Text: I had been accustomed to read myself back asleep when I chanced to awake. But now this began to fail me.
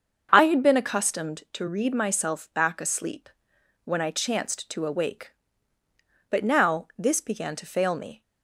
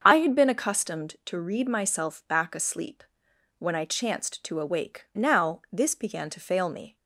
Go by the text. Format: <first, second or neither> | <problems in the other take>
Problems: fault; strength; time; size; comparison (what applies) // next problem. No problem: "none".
first | starts louder than the rest; until 1.0 s; 6.5 dB; also in the first // pauses between "asleep" and "when"; noticeable; at 3.0 s; 0.56 s long; noticeable in the first // skips "But"; at 5.1 s